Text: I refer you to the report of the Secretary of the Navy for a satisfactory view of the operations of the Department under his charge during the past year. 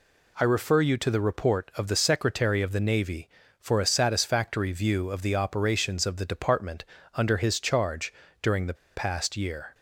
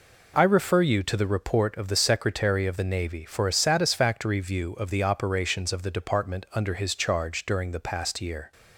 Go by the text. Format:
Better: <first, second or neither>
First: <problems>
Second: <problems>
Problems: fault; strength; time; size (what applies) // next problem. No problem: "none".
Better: second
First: pauses between "Department" and "under"; slight; at 6.8 s; 0.30 s long // pauses between "charge" and "during"; slight; at 8.1 s; 0.30 s long // pauses between "the" and "past"; slight; at 8.7 s; 0.20 s long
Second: none